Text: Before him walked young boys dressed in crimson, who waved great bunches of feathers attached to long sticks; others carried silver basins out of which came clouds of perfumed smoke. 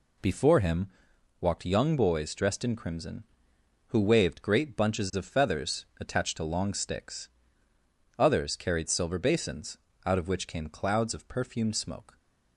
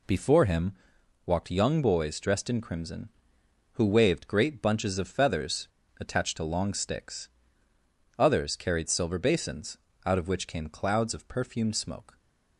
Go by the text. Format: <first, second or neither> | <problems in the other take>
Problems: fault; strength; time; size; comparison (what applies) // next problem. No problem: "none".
first | pauses between "him" and "walked"; noticeable; at 0.7 s; 0.52 s long; noticeable in the first // pauses between "feathers" and "attached"; slight; at 5.6 s; 0.31 s long // pauses between "basins" and "out"; slight; at 9.7 s; 0.26 s long; slight in the first